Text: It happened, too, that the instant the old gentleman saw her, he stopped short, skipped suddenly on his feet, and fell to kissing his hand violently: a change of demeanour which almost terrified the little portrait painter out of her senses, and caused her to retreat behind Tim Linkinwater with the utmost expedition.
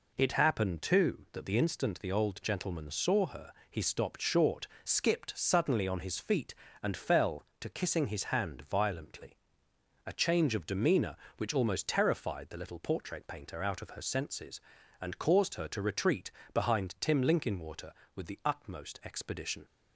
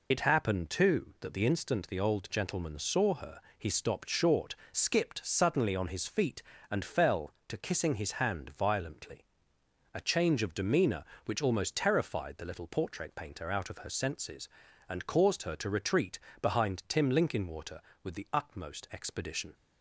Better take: first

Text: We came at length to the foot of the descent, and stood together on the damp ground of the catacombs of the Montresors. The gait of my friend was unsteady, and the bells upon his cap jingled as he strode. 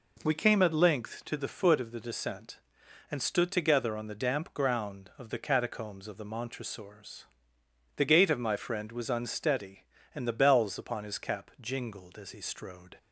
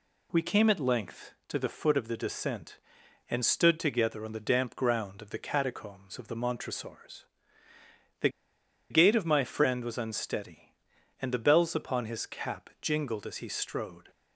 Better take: first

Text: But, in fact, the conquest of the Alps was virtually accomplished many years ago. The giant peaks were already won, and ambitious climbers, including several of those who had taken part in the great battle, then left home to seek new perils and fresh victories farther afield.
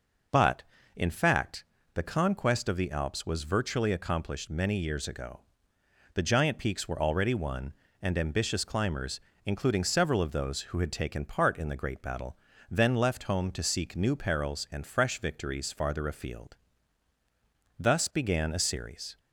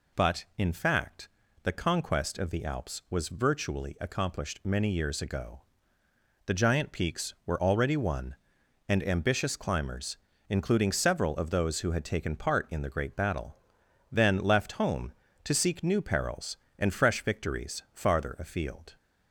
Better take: second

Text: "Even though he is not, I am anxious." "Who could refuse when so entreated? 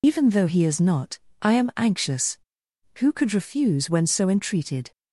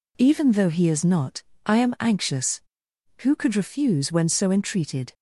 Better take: second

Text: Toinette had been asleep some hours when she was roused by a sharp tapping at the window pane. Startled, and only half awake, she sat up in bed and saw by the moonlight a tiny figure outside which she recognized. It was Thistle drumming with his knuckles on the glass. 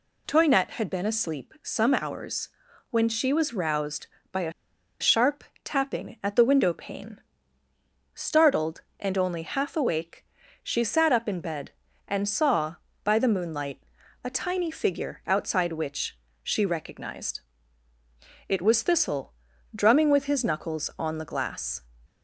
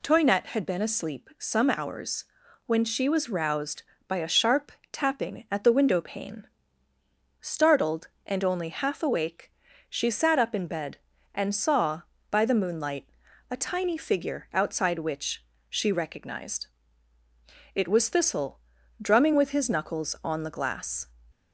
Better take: second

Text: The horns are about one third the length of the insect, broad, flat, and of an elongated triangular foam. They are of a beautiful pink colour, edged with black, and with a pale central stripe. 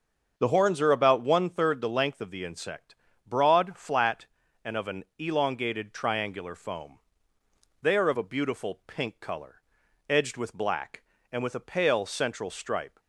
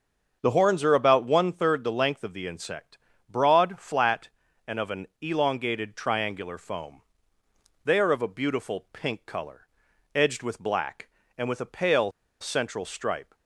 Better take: first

